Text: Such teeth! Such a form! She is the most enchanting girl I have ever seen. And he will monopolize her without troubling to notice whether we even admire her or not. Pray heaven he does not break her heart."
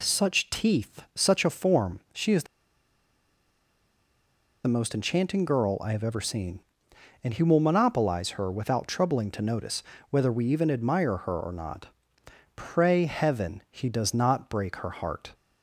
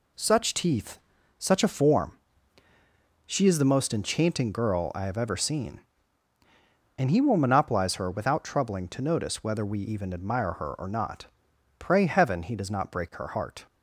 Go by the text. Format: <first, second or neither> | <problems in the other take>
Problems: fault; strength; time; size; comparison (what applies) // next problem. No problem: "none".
second | pauses between "the" and "most"; strong; at 2.4 s; 2.2 s long // pauses between "notice" and "whether"; slight; at 9.8 s; 0.26 s long